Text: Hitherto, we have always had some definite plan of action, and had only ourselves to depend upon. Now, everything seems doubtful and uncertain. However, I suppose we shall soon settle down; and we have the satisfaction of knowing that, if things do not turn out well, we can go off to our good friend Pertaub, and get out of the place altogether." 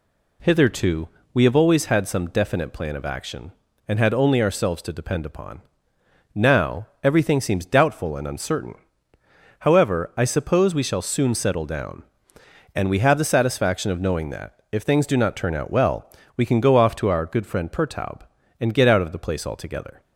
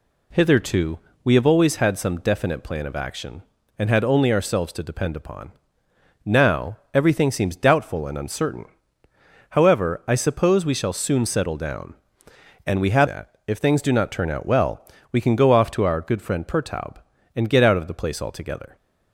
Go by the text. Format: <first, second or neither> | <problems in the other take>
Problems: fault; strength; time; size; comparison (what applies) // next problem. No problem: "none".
first | skips "the satisfaction of knowing"; at 13.0 s